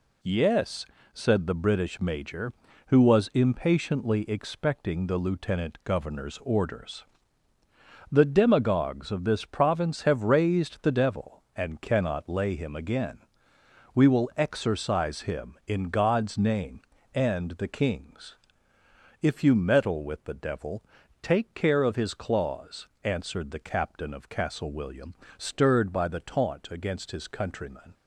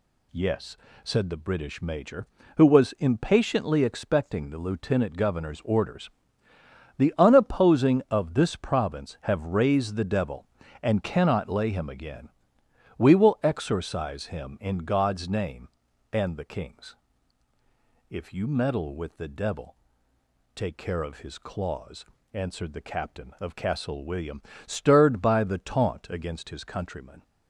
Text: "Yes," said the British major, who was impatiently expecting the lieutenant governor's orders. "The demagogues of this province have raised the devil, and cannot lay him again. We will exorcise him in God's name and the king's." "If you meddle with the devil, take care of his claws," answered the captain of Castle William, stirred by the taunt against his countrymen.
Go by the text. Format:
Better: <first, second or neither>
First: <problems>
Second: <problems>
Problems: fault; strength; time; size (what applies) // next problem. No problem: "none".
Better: first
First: none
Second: says "unopposing" for "demagogues"; at 7.1 s